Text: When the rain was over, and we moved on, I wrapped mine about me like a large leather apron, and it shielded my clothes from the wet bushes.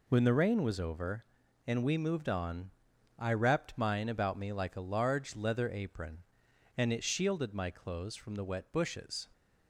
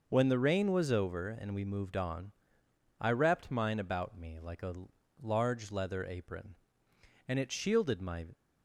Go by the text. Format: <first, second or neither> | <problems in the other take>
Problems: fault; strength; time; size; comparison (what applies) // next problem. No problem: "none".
first | pauses between "a" and "large"; noticeable; at 4.7 s; 0.48 s long // stops before "clothes from the wet bushes"; at 8.3 s